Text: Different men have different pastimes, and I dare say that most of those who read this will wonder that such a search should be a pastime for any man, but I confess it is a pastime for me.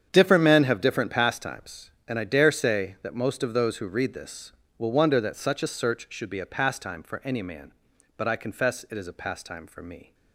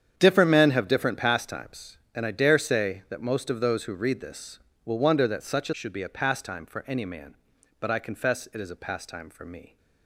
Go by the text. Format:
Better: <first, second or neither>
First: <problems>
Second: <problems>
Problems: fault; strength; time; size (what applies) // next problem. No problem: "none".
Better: first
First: starts louder than the rest; strong; until 1.1 s; 8.5 dB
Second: starts louder than the rest; strong; until 1.1 s; 8.5 dB // skips "search"; at 5.7 s